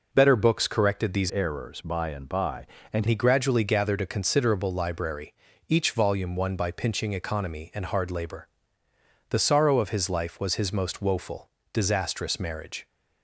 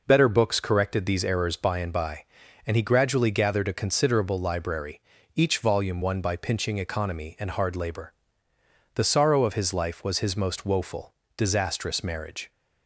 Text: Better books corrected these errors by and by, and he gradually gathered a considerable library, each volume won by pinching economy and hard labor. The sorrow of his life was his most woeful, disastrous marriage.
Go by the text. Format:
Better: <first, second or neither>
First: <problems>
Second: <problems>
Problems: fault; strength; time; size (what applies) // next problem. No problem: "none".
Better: second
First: changes voice from "errors" to "and"; from 1.2 to 3.0 s; 1.8 s long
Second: none